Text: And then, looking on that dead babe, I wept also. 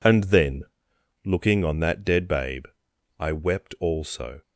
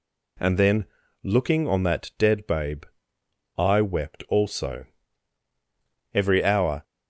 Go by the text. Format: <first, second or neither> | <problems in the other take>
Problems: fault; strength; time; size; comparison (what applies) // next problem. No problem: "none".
first | goes on to say "Every hour"; noticeable; from 6.1 s on; 0.70 s long